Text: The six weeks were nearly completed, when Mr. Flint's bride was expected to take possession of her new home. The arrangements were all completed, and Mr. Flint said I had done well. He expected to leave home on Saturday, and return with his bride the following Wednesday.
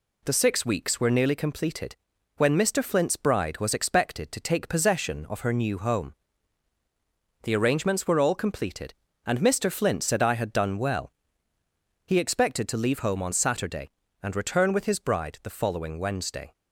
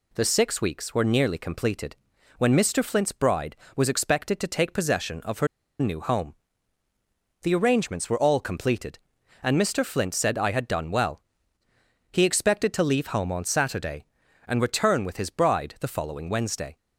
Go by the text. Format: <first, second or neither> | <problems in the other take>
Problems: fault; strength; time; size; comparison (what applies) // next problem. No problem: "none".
first | pauses between "her" and "new"; slight; at 5.4 s; 0.33 s long